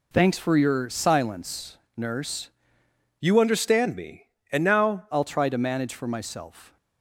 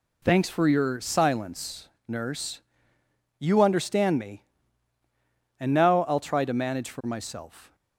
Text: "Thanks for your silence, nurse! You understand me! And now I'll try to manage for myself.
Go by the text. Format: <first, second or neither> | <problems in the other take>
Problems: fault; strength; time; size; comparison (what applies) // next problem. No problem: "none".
second | changes voice from "You" to "now"; from 3.1 to 5.0 s; 1.9 s long